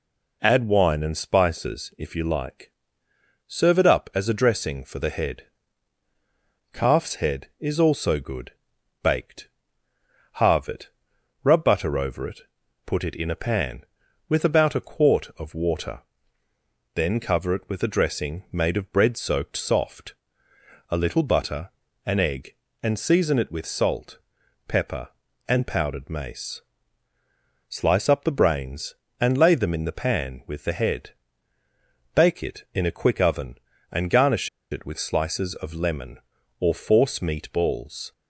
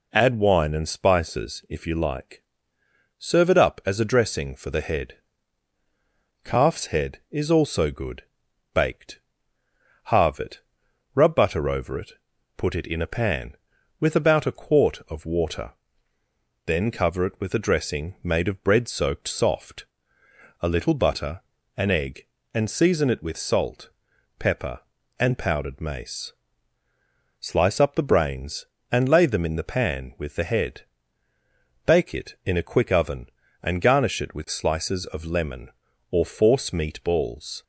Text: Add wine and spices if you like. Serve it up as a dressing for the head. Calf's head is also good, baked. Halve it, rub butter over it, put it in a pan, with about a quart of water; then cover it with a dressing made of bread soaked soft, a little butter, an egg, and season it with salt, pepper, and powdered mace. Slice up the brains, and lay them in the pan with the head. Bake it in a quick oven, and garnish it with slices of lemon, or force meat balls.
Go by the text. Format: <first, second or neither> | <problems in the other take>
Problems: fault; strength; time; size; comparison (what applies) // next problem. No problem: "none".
second | pauses between "garnish" and "it"; slight; at 34.4 s; 0.23 s long